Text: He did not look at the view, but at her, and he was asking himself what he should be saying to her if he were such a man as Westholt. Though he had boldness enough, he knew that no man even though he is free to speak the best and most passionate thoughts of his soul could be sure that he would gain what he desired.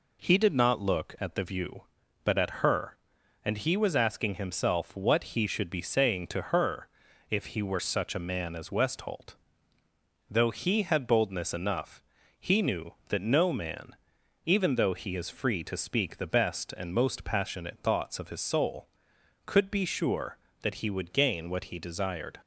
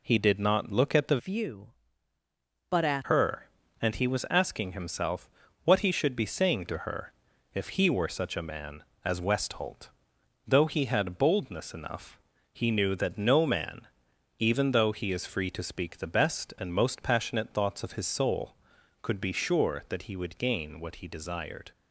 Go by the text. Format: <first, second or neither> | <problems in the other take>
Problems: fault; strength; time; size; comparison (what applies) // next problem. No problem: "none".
first | changes voice from "view" to "at"; from 1.1 to 3.0 s; 1.9 s long // pauses between "himself" and "what"; slight; at 5.2 s; 0.36 s long // pauses between "her" and "if"; at 7.1 s; 0.44 s long; also in the first // pauses between "man" and "even"; noticeable; at 13.8 s; 0.56 s long; noticeable in the first